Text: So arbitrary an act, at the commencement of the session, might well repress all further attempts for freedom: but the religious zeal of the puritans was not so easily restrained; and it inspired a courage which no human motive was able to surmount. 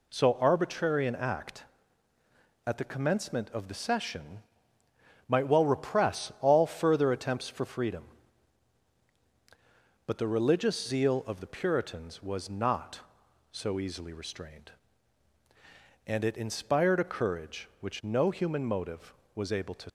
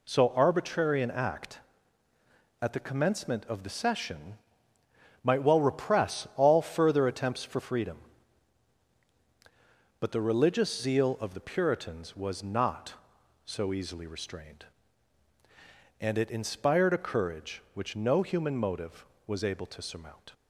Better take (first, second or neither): second